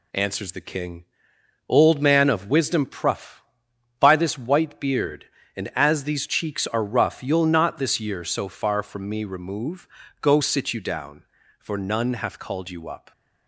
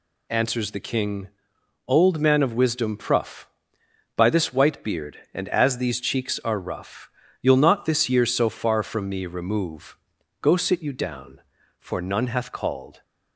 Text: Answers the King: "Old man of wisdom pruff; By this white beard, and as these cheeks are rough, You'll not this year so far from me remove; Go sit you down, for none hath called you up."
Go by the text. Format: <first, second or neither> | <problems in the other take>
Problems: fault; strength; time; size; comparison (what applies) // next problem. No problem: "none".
first | stops before "you up"; at 13.0 s